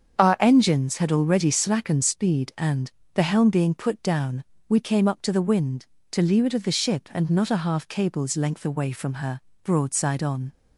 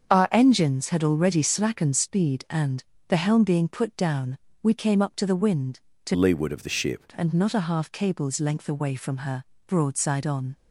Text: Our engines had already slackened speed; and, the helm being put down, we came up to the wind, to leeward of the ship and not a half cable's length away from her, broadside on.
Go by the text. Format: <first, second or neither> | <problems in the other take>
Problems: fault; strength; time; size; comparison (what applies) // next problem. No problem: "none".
first | starts louder than the rest; until 1.1 s; 7 dB; also in the first // changes voice from "leeward" to "ship"; from 6.1 to 7.0 s; 0.9 s long